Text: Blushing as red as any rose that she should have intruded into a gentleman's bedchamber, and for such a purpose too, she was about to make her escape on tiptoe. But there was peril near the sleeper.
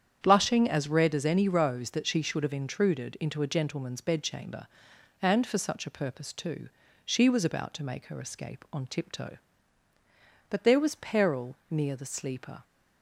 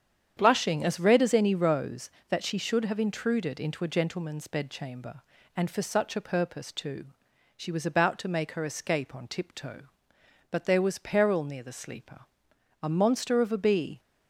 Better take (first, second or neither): first